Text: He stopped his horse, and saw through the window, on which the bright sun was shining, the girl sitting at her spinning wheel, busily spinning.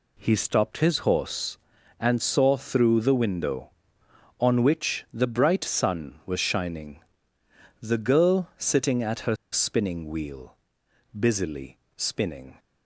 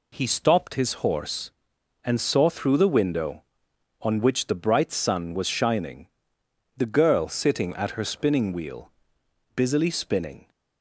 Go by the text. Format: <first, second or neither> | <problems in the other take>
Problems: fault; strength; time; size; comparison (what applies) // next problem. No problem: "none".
second | pauses between "her" and "spinning"; slight; at 9.3 s; 0.16 s long // pauses between "busily" and "spinning"; slight; at 11.7 s; 0.18 s long